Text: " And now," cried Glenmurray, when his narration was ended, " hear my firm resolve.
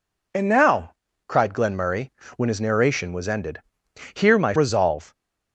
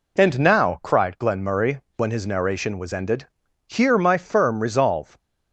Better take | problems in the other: second | skips "firm"; at 4.5 s

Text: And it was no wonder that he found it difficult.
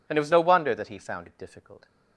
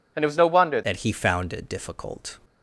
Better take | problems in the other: first | changes voice at "that"; from 0.8 s on; 1.5 s long

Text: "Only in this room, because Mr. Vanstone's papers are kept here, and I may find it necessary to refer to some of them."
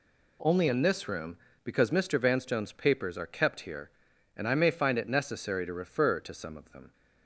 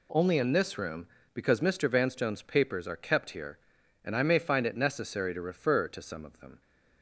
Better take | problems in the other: neither | none

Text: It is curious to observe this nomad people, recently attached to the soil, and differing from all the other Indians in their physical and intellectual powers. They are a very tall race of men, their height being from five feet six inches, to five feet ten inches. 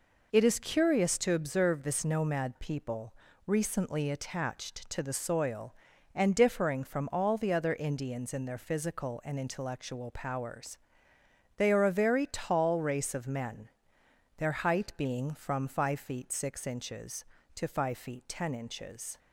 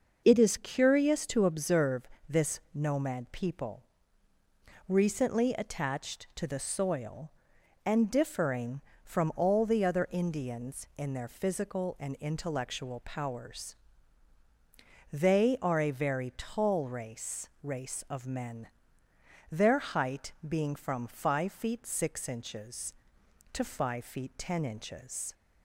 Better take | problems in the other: first | pauses between "observe" and "this"; slight; at 2.0 s; 0.22 s long // says "race" twice; at 17.6 s // pauses between "height" and "being"; slight; at 20.3 s; 0.16 s long

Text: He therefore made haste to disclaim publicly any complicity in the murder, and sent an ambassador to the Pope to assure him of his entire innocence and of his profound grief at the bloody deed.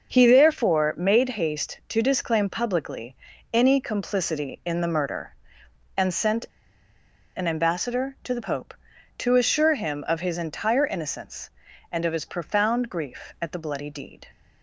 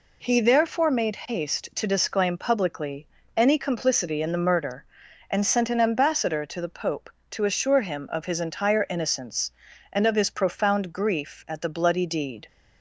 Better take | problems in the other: second | starts louder than the rest; noticeable; until 1.1 s; 6 dB // pauses between "publicly" and "any"; at 3.1 s; 0.38 s long; slight in the second // pauses between "sent" and "an"; noticeable; at 6.4 s; 0.91 s long

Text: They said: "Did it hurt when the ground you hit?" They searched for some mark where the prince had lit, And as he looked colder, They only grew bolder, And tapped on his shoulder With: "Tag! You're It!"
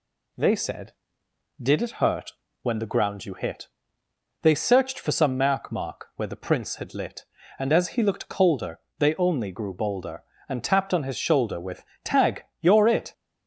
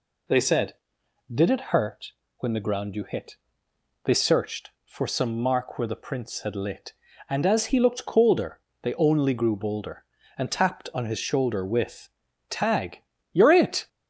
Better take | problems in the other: second | pauses between "hurt" and "when"; slight; at 2.3 s; 0.32 s long; slight in the second // says "mark" twice; at 5.7 s

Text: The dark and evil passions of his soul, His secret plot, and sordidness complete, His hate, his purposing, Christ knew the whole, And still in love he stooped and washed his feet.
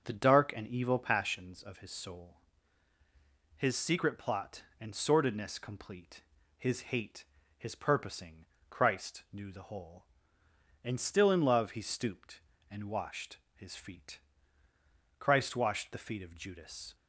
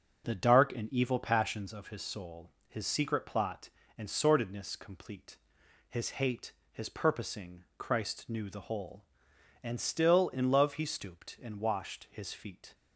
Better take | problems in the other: second | starts louder than the rest; until 1.1 s; 6.5 dB; noticeable in the second // pauses between "washed" and "his"; slight; at 13.3 s; 0.18 s long // goes on to say "Christ washed the feet of Judas"; strong; from 15.1 s on; 1.7 s long

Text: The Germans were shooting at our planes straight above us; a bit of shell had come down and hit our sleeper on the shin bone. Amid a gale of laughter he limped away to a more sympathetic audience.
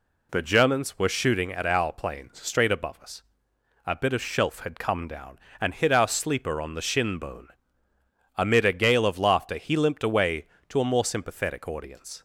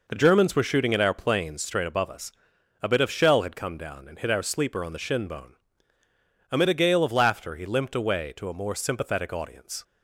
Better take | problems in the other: second | says "shelf" for "shell"; at 4.2 s

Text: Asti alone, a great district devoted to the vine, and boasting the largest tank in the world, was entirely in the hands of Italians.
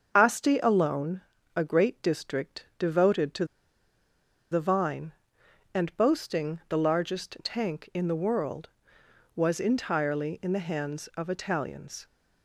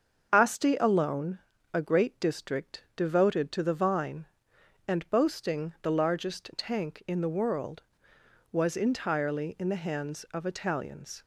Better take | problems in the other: second | starts louder than the rest; until 1.1 s; 6.5 dB; also in the second // pauses between "to" and "the"; at 3.4 s; 1.0 s long

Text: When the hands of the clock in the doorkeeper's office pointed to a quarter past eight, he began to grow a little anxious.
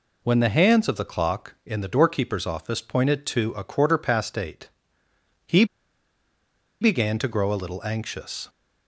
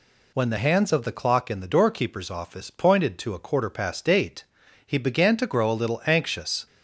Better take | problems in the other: second | pauses between "he" and "began"; at 5.6 s; 1.1 s long

